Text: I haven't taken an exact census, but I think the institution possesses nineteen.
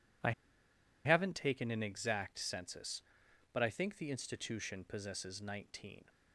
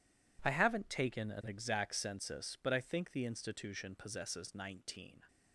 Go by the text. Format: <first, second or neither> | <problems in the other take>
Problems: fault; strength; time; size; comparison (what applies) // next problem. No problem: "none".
second | pauses between "I" and "haven't"; noticeable; at 0.3 s; 0.73 s long